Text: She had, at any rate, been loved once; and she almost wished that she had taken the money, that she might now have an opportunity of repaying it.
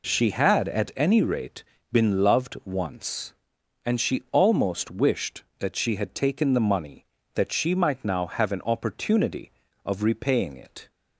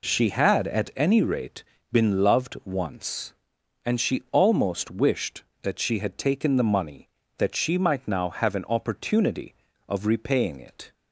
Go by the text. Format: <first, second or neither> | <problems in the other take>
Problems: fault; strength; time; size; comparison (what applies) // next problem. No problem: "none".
neither | none